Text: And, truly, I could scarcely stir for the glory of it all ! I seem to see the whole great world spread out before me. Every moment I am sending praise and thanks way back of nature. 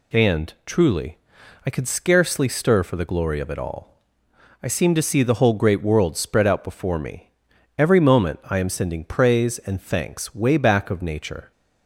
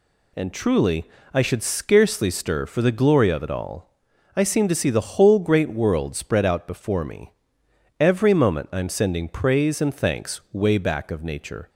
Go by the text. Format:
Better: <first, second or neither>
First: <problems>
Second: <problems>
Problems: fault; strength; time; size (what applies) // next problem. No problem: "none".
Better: first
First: none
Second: says "should" for "could"; at 1.4 s